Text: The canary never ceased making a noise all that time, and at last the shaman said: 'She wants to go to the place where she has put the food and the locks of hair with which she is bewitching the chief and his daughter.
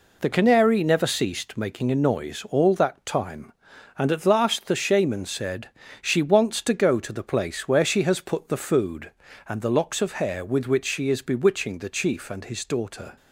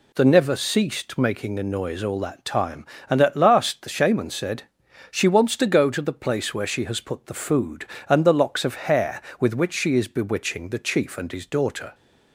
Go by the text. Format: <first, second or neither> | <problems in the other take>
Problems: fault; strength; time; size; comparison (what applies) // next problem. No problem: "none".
first | skips "canary"; at 0.2 s